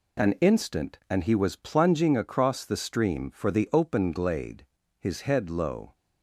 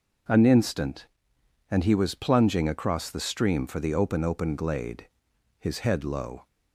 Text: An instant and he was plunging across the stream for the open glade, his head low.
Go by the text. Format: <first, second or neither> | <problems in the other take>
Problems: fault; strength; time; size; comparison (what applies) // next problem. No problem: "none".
first | says "open" twice; at 4.2 s